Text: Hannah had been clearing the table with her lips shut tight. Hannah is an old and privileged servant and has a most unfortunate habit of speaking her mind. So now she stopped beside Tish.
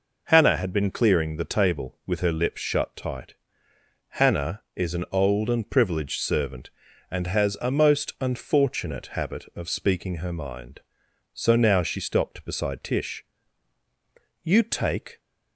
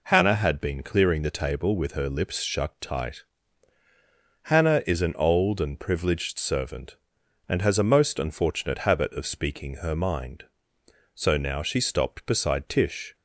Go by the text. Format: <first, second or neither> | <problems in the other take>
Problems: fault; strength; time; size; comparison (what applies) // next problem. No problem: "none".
second | goes on to say "You take"; noticeable; from 14.4 s on; 0.78 s long